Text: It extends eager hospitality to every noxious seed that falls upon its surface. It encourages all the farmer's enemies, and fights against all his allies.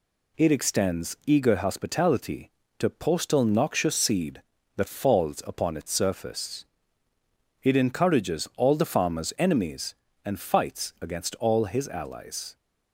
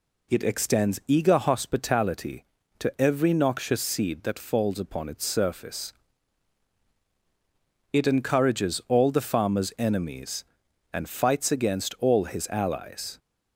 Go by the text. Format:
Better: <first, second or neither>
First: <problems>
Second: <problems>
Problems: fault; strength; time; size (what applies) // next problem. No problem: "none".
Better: second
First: says "postal" for "every"; at 2.8 s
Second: none